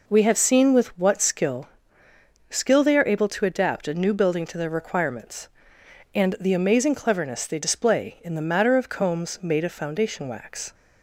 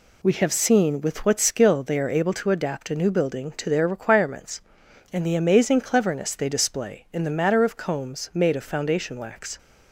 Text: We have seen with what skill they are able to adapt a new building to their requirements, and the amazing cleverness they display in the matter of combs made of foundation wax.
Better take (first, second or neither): second